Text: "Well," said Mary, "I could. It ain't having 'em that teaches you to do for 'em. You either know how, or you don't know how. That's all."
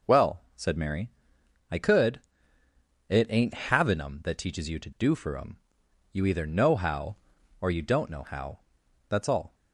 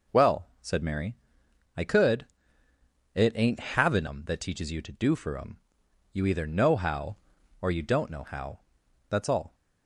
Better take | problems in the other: neither | none

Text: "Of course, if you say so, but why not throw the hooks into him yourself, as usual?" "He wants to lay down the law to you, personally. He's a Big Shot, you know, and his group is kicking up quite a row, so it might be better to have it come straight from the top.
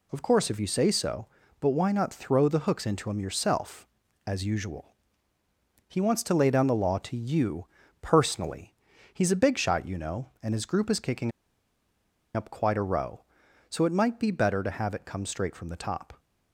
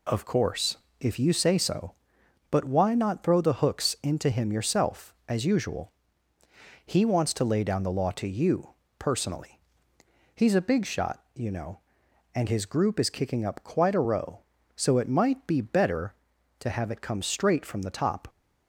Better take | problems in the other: second | pauses between "kicking" and "up"; at 11.3 s; 1.0 s long

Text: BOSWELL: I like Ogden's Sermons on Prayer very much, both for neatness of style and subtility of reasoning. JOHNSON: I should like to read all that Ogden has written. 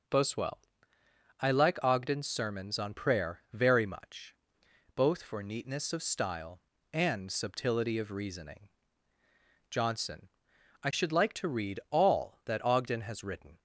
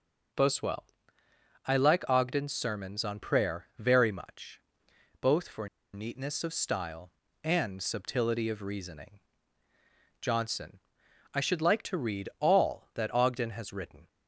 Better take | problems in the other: first | pauses between "for" and "neatness"; slight; at 5.6 s; 0.25 s long

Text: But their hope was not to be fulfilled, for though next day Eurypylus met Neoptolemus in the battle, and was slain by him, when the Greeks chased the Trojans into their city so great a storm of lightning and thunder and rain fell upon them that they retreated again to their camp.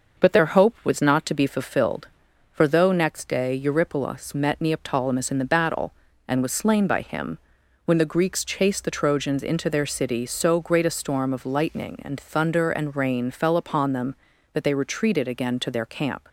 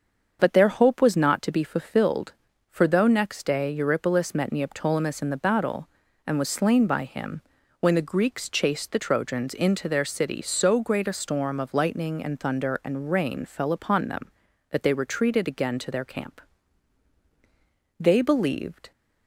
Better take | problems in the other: first | starts louder than the rest; until 1.4 s; 7 dB; noticeable in the first // goes on to say "They believed"; noticeable; from 17.9 s on; 0.92 s long

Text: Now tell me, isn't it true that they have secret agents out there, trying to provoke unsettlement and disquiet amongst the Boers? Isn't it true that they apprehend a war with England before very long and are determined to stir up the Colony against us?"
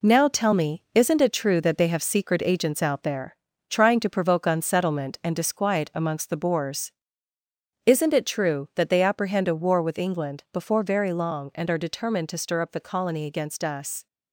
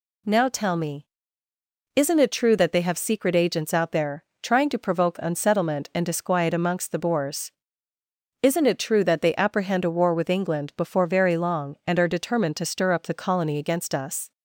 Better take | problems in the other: second | gets quieter; throughout; 6.5 dB

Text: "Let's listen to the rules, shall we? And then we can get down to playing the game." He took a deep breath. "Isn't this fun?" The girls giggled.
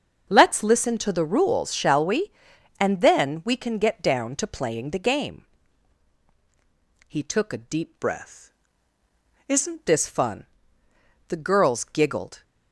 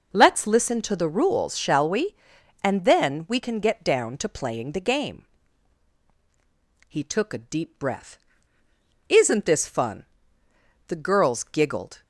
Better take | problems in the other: second | starts louder than the rest; until 1.3 s; 6.5 dB // changes voice from "breath" to "Isn't"; from 7.9 to 9.8 s; 1.9 s long

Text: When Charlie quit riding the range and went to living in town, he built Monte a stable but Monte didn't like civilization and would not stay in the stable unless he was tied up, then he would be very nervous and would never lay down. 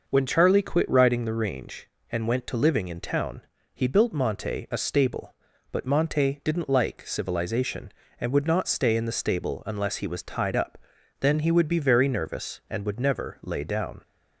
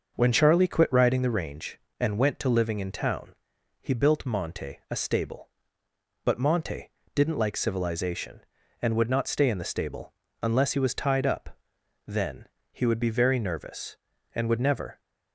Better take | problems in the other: first | starts louder than the rest; noticeable; until 1.1 s; 6 dB // pauses between "Monte" and "didn't"; slight; at 6.8 s; 0.24 s long // pauses between "stable" and "unless"; slight; at 10.1 s; 0.28 s long // pauses between "then" and "he"; slight; at 12.4 s; 0.24 s long // stops before "lay down"; at 14.9 s

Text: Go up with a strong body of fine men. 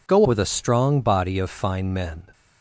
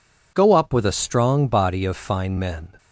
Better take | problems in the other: second | skips "up"; at 0.2 s

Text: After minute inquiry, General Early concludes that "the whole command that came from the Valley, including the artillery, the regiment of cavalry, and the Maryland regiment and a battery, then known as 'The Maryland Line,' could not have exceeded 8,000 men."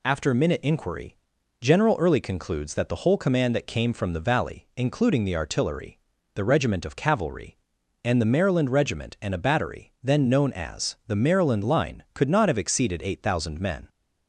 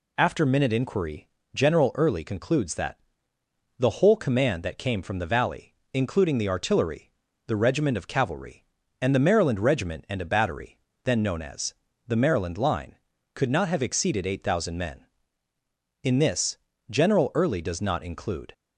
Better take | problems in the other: first | pauses between "that" and "the"; noticeable; at 2.9 s; 0.80 s long // pauses between "as" and "The"; slight; at 11.7 s; 0.36 s long // goes on to say "In this General Early does not include"; strong; from 16.0 s on; 2.5 s long

